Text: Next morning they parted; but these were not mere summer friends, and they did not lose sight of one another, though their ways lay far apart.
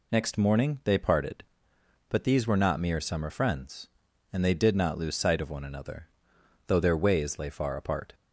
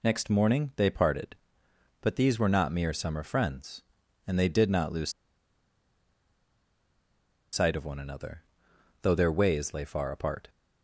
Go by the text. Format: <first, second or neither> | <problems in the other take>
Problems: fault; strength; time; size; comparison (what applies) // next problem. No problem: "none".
first | pauses between "lose" and "sight"; strong; at 5.1 s; 2.4 s long